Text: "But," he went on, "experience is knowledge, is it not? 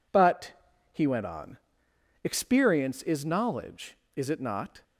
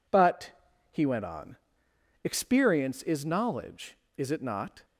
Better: neither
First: none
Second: none

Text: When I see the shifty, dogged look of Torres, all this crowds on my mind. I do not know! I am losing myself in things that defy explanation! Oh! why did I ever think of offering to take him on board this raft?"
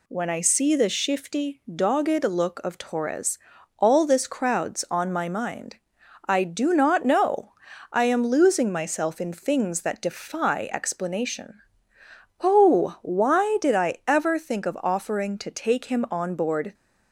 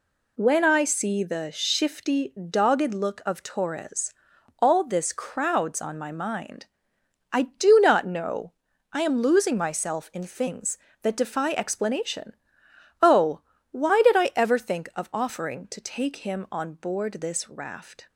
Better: second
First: stops before "this raft"; at 16.7 s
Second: none

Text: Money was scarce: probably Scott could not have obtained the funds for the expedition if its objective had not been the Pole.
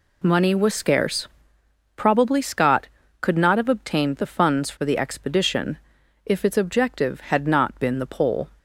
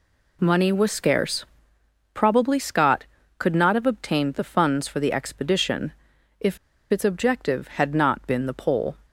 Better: first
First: pauses between "expedition" and "if"; noticeable; at 5.7 s; 0.48 s long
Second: pauses between "expedition" and "if"; noticeable; at 5.9 s; 0.48 s long // pauses between "if" and "its"; slight; at 6.5 s; 0.32 s long

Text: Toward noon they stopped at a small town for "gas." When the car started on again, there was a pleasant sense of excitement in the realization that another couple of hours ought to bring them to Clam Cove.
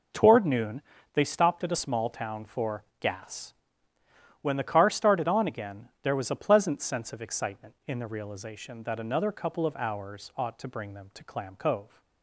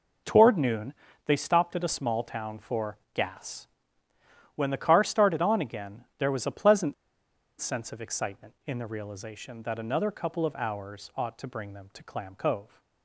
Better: first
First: pauses between "noon" and "they"; slight; at 0.8 s; 0.32 s long // pauses between "for" and "gas"; slight; at 2.8 s; 0.16 s long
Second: pauses between "noon" and "they"; slight; at 0.9 s; 0.32 s long // pauses between "for" and "gas"; slight; at 2.9 s; 0.16 s long // pauses between "pleasant" and "sense"; noticeable; at 6.9 s; 0.66 s long

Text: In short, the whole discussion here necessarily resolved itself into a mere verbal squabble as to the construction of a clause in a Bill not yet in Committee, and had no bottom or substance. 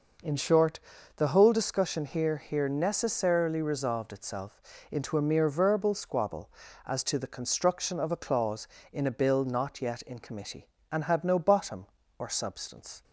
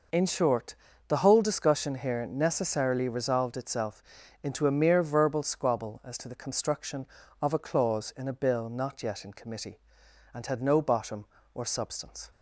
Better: second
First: says "here" twice; at 2.3 s // pauses between "itself" and "into"; slight; at 4.5 s; 0.30 s long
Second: pauses between "itself" and "into"; at 4.0 s; 0.40 s long

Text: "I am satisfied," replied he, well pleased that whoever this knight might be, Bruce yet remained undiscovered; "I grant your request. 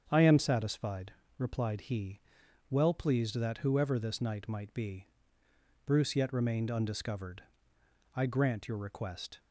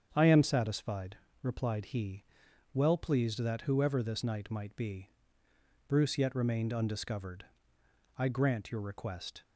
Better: neither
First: starts louder than the rest; strong; until 1.1 s; 7.5 dB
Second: starts louder than the rest; strong; until 1.1 s; 7.5 dB

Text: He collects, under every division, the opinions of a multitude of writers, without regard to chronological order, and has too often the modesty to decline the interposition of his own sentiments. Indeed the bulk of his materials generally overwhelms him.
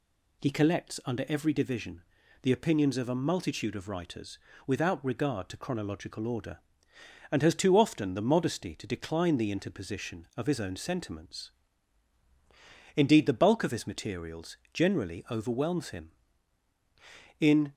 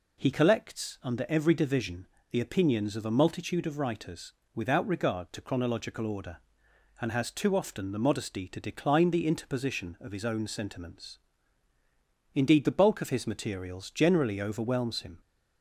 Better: second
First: pauses between "materials" and "generally"; slight; at 14.5 s; 0.16 s long // goes on to say "In"; slight; from 17.3 s on; 0.34 s long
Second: none

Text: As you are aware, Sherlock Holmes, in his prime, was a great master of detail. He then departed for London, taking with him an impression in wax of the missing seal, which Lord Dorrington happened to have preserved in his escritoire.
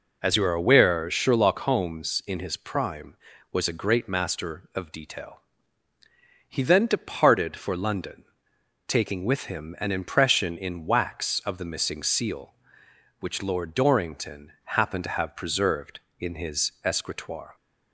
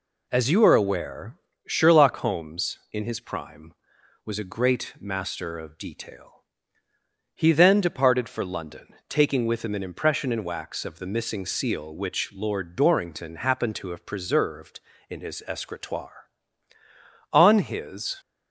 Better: first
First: none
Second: goes on to say "On his"; noticeable; from 17.3 s on; 0.86 s long

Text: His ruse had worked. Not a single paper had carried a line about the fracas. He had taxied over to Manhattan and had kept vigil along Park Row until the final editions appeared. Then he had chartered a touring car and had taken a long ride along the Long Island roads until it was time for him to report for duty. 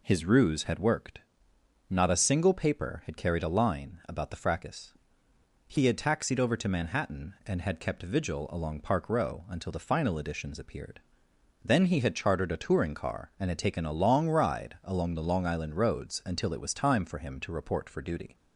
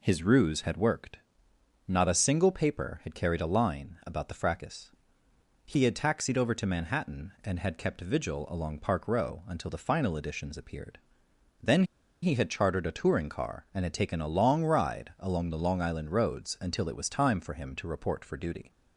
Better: first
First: none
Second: pauses between "Then" and "he"; at 11.8 s; 0.39 s long

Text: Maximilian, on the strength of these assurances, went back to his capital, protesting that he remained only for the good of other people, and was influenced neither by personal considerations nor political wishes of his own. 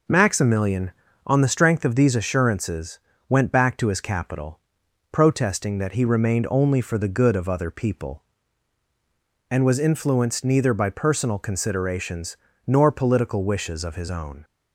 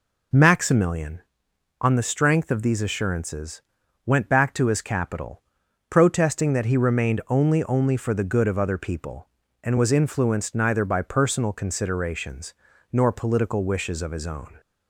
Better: first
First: pauses between "considerations" and "nor"; slight; at 12.3 s; 0.32 s long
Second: says "only" twice; at 7.6 s // pauses between "considerations" and "nor"; at 12.5 s; 0.38 s long

